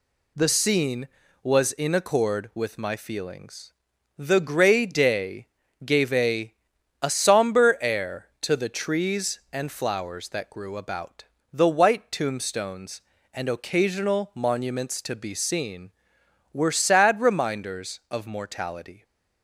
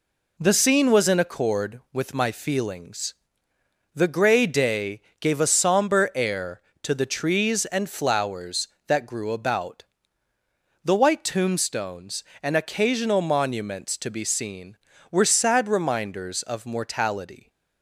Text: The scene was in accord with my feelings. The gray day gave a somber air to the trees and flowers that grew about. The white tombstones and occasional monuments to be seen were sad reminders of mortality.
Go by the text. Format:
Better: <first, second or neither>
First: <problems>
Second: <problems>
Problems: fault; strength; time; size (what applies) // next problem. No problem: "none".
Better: second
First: pauses between "day" and "gave"; at 5.4 s; 0.38 s long // says "a" twice; at 7.0 s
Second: pauses between "day" and "gave"; slight; at 5.0 s; 0.18 s long